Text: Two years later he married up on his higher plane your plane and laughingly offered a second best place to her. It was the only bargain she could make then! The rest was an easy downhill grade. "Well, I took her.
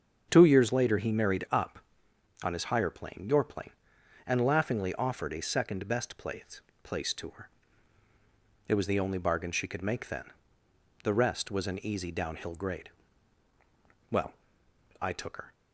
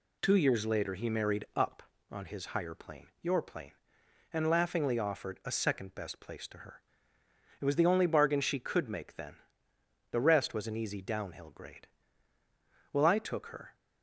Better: second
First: starts louder than the rest; strong; until 1.3 s; 7 dB // says "place" twice; at 6.8 s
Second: none

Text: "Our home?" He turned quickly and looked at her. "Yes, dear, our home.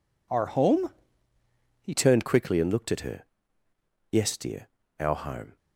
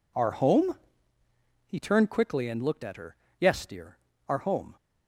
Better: second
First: changes voice at "turned"; from 1.9 s on; 3.6 s long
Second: none

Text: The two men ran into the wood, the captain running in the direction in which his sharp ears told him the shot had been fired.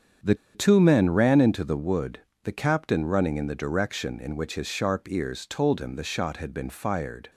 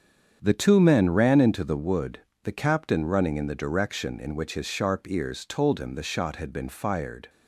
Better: second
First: starts louder than the rest; strong; until 1.4 s; 8 dB // pauses between "The" and "two"; slight; at 0.3 s; 0.19 s long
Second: starts louder than the rest; strong; until 1.4 s; 8 dB

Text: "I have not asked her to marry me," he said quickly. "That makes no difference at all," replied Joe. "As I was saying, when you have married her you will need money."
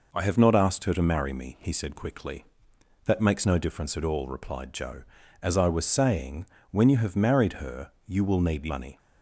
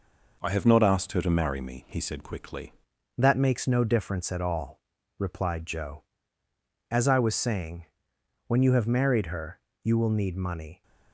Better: first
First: pauses between "her" and "you"; slight; at 7.9 s; 0.16 s long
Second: changes voice at "That"; from 3.1 s on; 7.7 s long // pauses between "her" and "you"; slight; at 9.6 s; 0.24 s long

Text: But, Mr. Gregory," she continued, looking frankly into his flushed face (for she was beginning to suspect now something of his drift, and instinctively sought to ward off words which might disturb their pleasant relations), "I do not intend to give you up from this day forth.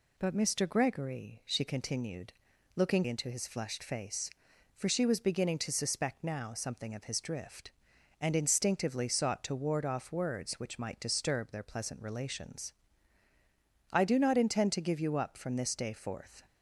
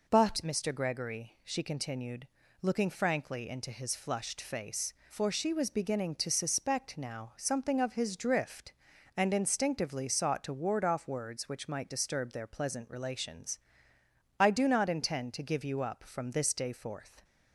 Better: second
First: skips "frankly"; at 3.0 s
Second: none

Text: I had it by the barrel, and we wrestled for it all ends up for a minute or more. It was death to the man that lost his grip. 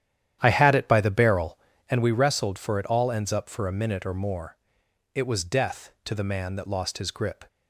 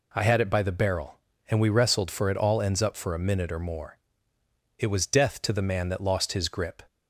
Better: second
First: starts louder than the rest; strong; until 2.0 s; 11 dB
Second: none

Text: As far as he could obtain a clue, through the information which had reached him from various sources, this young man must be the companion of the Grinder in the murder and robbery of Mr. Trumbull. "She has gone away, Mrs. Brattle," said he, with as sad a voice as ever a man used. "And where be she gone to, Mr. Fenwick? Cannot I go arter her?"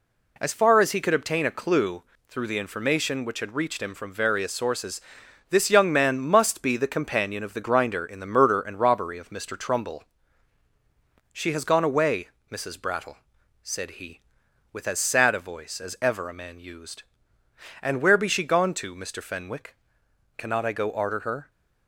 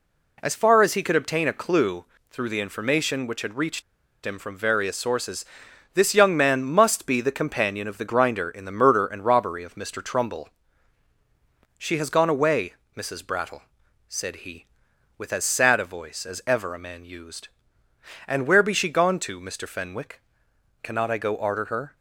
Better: first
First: none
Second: pauses between "reached" and "him"; at 3.8 s; 0.42 s long

